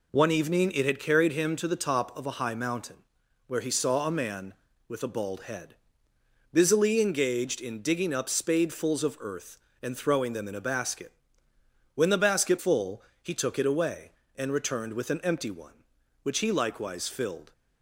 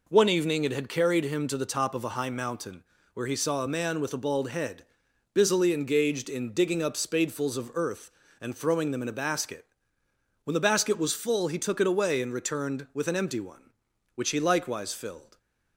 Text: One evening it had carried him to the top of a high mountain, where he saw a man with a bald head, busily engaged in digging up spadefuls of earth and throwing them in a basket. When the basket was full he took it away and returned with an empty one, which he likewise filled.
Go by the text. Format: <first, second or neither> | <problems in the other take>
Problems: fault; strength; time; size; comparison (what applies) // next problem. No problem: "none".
second | skips "was"; at 12.5 s // pauses between "full" and "he"; slight; at 13.0 s; 0.20 s long